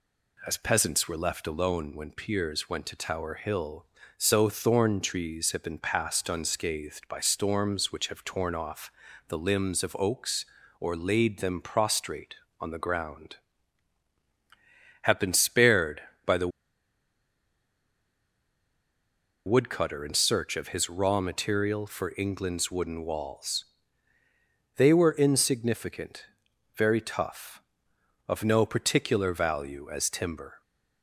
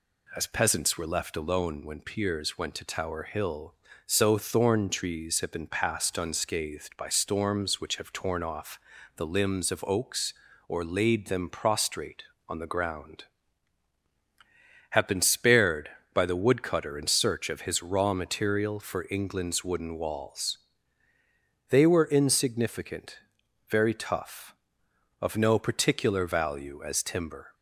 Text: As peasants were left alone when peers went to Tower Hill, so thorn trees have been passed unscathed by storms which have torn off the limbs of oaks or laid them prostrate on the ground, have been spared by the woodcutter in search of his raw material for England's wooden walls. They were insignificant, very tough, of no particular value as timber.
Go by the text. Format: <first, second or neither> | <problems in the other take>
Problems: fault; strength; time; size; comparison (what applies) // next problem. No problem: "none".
second | pauses between "off" and "the"; at 8.9 s; 0.38 s long; also in the second // pauses between "the" and "woodcutter"; strong; at 16.4 s; 2.9 s long